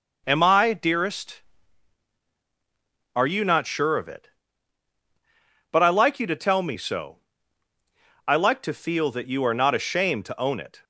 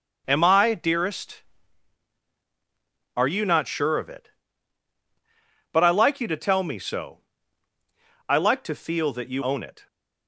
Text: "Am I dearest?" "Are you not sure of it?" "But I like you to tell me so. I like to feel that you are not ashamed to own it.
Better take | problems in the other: first | skips "are not ashamed to"; at 9.4 s

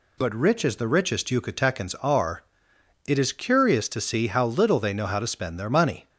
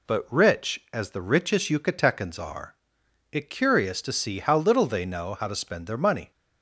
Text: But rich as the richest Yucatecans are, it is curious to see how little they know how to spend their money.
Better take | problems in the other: first | skips "is"; at 3.5 s

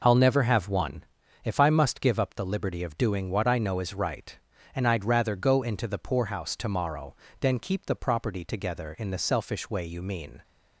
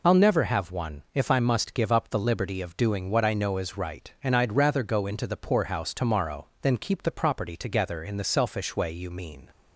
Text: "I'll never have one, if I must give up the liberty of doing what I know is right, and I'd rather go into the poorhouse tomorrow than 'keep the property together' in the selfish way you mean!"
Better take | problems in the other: first | loses the start of "I'll"; at 0.0 s; 45 ms

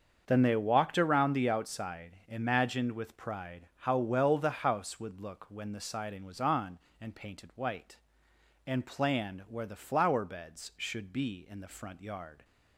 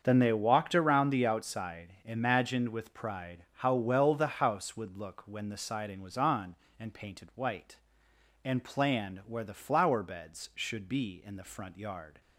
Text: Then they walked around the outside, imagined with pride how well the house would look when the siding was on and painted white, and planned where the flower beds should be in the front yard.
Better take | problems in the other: neither | starts louder than the rest; the same in both

